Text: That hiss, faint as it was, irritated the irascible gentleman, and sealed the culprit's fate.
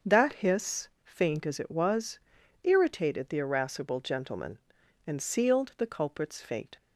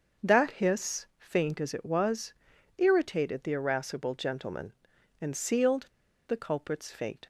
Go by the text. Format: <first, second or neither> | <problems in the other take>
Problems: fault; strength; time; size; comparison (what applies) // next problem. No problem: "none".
first | starts louder than the rest; until 1.3 s; 6.5 dB; also in the first // pauses between "sealed" and "the"; at 5.8 s; 0.41 s long